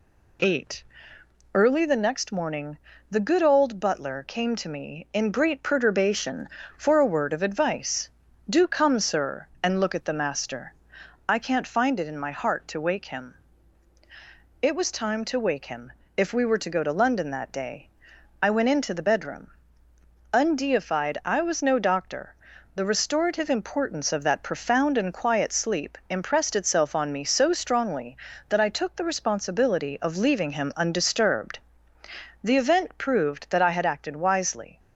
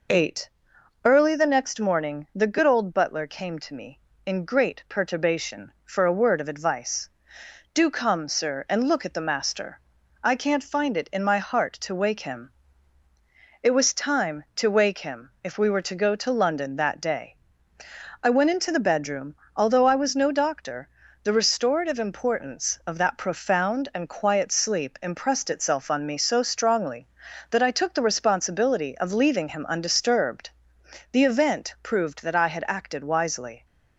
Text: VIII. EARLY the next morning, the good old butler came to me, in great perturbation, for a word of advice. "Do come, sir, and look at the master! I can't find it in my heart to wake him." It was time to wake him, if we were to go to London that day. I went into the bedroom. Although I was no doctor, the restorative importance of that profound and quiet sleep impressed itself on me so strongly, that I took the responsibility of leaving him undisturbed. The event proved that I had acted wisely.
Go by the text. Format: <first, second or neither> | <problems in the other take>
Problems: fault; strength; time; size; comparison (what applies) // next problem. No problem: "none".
second | says "Undeified" for "Although"; at 20.3 s